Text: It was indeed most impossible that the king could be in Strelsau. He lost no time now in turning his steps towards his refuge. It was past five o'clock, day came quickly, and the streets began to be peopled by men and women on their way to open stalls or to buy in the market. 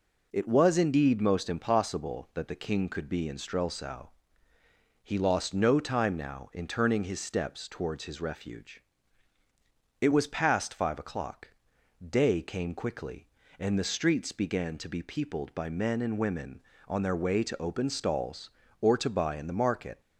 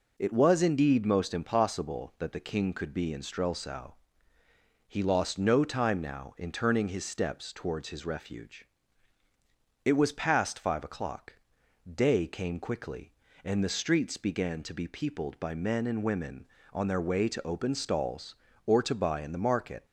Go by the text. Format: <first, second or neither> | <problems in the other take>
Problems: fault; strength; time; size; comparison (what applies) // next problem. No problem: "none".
neither | none